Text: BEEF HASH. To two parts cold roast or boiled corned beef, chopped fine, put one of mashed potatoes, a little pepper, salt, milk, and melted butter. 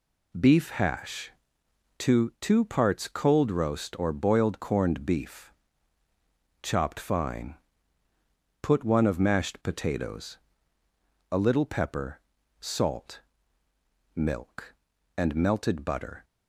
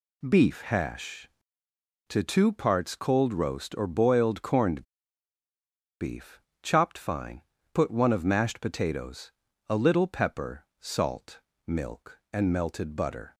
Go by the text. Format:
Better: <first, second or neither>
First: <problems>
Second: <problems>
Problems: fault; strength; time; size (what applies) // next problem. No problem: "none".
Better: first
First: none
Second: pauses between "corned" and "beef"; at 4.8 s; 1.1 s long